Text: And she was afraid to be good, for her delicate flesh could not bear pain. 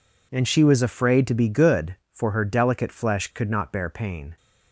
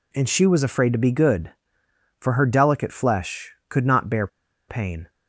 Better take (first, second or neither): first